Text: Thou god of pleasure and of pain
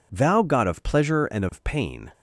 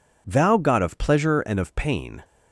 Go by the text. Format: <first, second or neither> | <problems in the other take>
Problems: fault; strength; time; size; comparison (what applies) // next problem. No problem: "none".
neither | none